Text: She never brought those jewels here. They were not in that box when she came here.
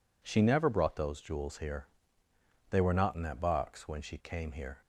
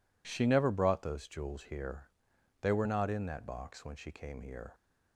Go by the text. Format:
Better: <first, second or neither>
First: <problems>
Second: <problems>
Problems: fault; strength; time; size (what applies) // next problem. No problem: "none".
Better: neither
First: none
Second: none